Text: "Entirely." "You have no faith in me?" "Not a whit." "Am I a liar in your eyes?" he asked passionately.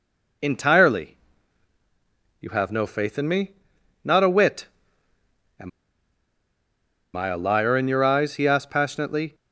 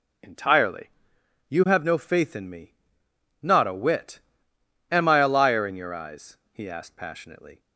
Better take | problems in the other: second | pauses between "Am" and "I"; strong; at 5.6 s; 1.4 s long

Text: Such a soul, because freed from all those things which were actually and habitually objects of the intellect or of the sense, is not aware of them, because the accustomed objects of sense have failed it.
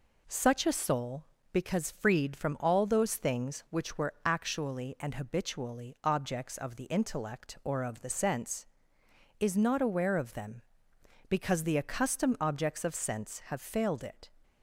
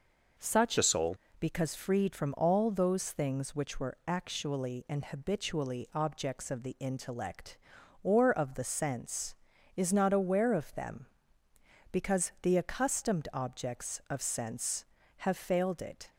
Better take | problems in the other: first | changes voice from "a" to "soul"; from 0.7 to 1.1 s; 0.4 s long

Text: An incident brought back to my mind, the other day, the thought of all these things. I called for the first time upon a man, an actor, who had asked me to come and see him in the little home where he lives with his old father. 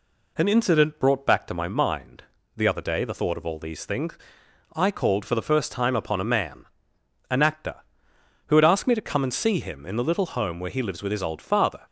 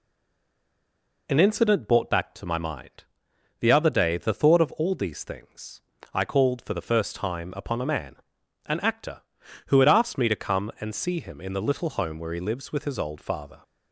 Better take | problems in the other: first | stays silent before the first word; noticeable; until 1.2 s; 1.2 s long

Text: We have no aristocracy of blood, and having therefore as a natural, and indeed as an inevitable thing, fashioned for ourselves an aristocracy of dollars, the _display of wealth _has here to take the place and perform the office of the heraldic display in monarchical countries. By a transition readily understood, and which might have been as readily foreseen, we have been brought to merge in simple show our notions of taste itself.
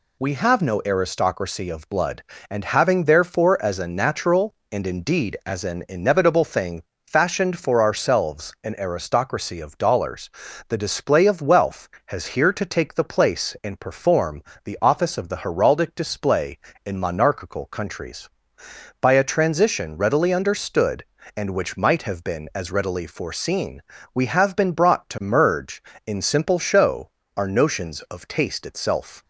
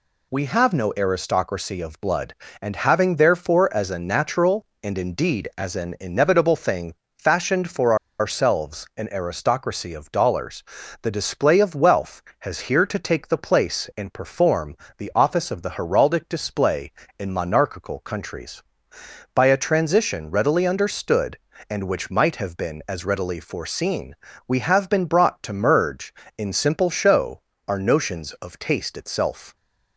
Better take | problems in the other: first | pauses between "for" and "ourselves"; slight; at 7.9 s; 0.24 s long // pauses between "perform" and "the"; slight; at 14.7 s; 0.22 s long; slight in the first // pauses between "show" and "our"; slight; at 27.4 s; 0.28 s long; slight in the first

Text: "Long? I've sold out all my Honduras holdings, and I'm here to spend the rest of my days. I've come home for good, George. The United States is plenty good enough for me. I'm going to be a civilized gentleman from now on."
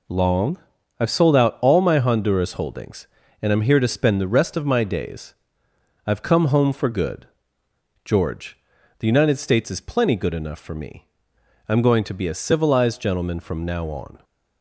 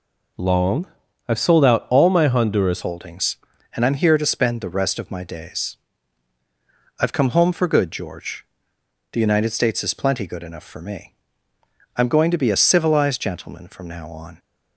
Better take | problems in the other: first | changes voice at "holdings"; from 2.8 s on; 11.5 s long

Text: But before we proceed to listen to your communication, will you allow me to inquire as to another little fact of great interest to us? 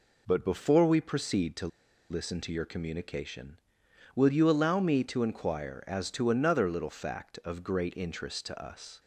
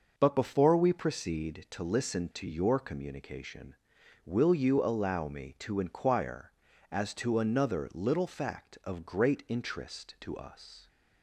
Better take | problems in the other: second | pauses between "to" and "listen"; at 1.6 s; 0.42 s long

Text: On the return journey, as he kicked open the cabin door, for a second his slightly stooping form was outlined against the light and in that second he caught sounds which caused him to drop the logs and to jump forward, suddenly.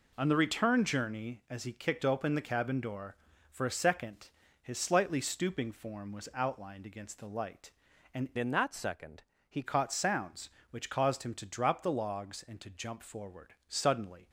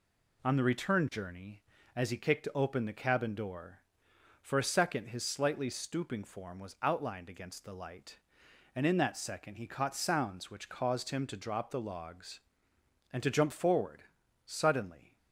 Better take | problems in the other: second | pauses between "second" and "his"; slight; at 4.2 s; 0.32 s long // changes voice from "in" to "he"; from 8.3 to 9.6 s; 1.3 s long // pauses between "second" and "he"; slight; at 9.2 s; 0.26 s long

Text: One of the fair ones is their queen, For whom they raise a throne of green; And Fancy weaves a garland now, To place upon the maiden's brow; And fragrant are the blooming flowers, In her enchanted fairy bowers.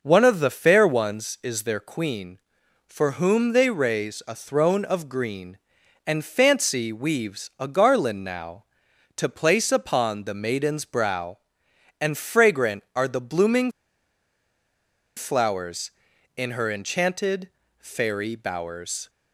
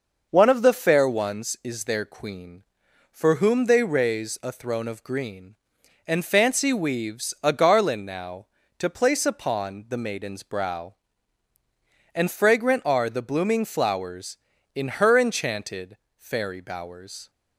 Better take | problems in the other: second | pauses between "blooming" and "flowers"; strong; at 13.7 s; 1.4 s long // pauses between "enchanted" and "fairy"; slight; at 17.4 s; 0.28 s long; slight in the second

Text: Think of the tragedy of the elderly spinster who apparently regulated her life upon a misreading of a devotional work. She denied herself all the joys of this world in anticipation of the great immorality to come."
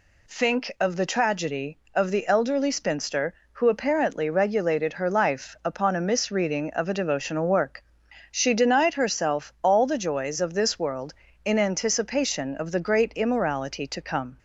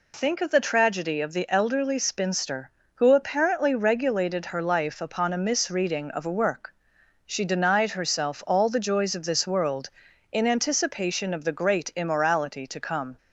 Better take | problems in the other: first | skips "devotional"; at 6.3 s

